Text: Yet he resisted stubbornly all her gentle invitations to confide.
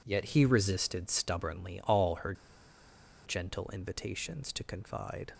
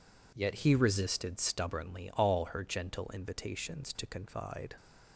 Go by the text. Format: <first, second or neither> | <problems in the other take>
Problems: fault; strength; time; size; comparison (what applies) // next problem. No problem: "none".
second | pauses between "her" and "gentle"; noticeable; at 2.3 s; 0.92 s long